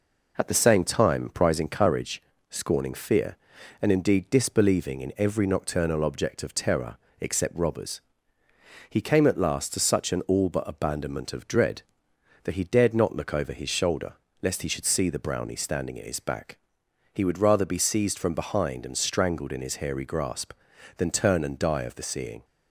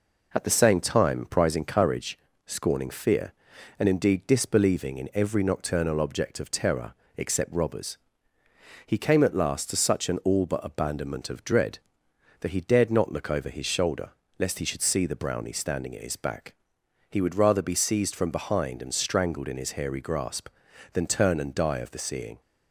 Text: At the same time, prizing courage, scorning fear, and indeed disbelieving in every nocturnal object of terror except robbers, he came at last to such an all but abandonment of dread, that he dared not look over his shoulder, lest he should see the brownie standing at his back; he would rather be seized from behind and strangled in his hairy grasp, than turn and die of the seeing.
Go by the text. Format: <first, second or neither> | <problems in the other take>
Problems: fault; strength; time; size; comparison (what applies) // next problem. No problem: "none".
neither | pauses between "terror" and "except"; slight; the same in both